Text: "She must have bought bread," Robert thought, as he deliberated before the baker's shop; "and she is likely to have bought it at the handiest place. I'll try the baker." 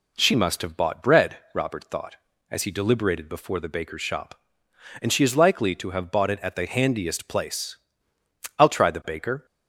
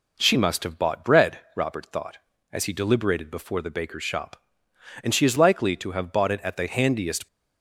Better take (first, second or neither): first